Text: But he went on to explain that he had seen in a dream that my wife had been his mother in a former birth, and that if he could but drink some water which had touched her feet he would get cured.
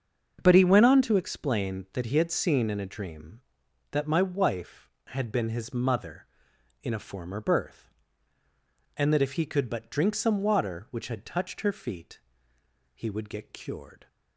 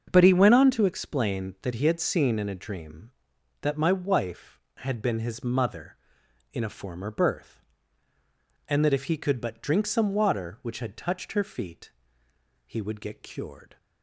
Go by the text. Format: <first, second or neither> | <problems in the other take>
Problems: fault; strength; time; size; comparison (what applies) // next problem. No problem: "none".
neither | starts louder than the rest; the same in both // pauses between "feet" and "he"; noticeable; the same in both